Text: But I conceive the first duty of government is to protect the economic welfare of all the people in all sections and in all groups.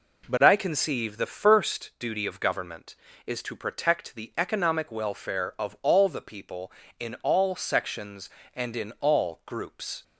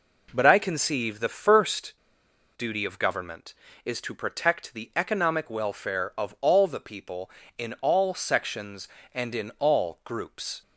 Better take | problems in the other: first | pauses between "first" and "duty"; noticeable; at 1.9 s; 0.64 s long

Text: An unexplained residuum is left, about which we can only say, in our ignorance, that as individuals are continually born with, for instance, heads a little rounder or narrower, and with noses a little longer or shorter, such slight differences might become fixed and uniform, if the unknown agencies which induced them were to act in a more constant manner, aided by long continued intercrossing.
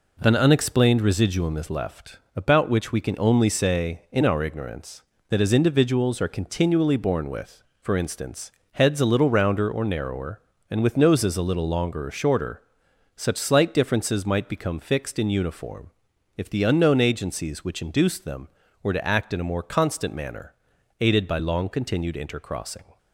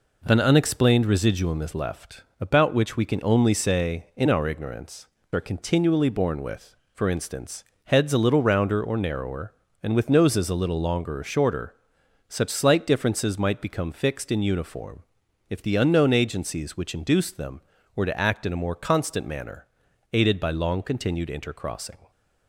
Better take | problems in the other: first | skips "that as individuals"; at 5.1 s

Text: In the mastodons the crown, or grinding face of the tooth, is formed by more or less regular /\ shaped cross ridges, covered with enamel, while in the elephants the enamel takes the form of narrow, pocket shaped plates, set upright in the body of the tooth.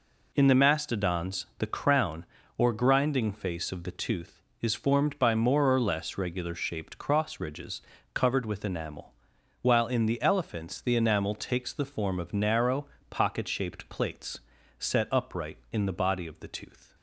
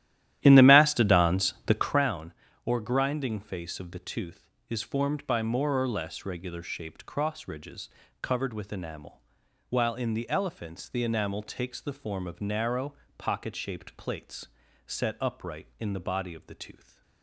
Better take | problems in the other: first | starts louder than the rest; strong; until 2.1 s; 12.5 dB

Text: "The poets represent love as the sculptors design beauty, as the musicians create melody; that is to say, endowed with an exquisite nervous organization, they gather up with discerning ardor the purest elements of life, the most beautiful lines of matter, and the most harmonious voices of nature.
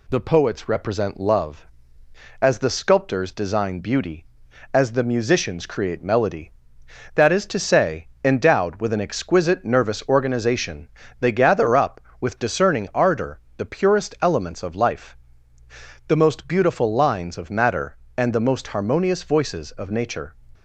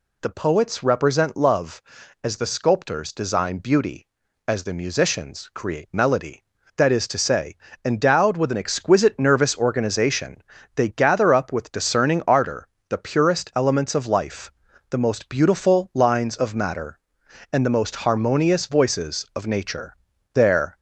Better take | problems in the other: first | pauses between "ardor" and "the"; slight; at 12.6 s; 0.22 s long; slight in the first // goes on to say "There"; slight; from 20.3 s on; 0.46 s long

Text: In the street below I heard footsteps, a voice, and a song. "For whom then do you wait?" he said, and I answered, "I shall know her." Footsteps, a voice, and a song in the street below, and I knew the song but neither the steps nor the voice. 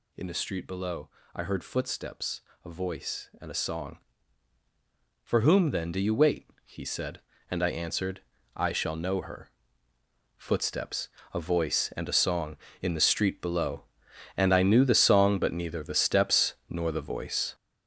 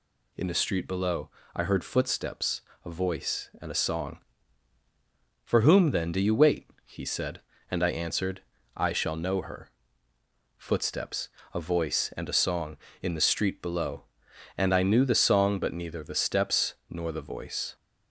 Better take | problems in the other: second | gets louder; strong; throughout; 8 dB // pauses between "below" and "I"; slight; at 1.0 s; 0.26 s long; slight in the second // pauses between "steps" and "nor"; slight; at 16.5 s; 0.16 s long; slight in the second

